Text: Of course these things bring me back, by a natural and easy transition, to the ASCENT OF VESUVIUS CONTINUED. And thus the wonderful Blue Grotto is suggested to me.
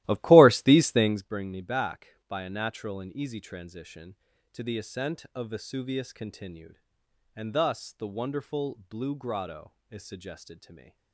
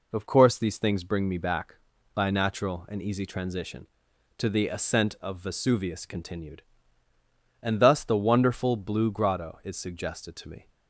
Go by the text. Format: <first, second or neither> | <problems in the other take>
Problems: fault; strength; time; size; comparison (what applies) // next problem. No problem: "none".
second | starts louder than the rest; strong; until 1.3 s; 15.5 dB